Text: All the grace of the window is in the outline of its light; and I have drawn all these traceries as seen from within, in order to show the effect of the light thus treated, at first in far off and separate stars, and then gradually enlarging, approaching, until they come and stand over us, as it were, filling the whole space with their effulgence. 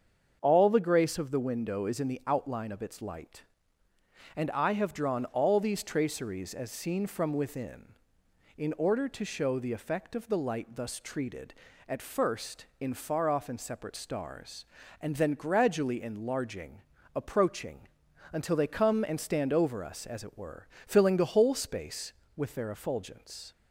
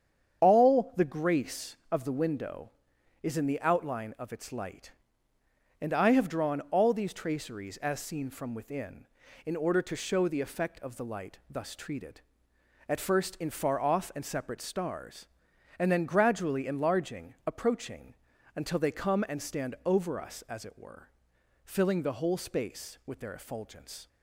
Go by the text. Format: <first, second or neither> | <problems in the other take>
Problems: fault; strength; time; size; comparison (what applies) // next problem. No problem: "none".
neither | starts louder than the rest; the same in both